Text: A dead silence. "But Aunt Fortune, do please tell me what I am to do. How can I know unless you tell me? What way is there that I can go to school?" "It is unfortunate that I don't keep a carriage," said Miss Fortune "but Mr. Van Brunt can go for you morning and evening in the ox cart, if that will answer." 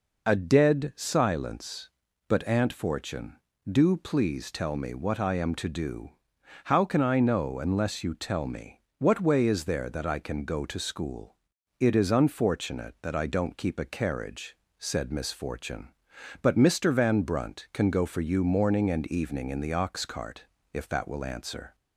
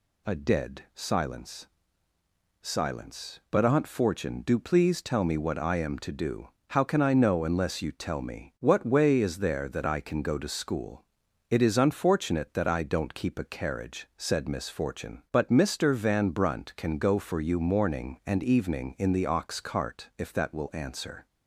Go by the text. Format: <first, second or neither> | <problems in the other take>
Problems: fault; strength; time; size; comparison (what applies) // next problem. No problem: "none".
first | says "silence" twice; at 2.6 s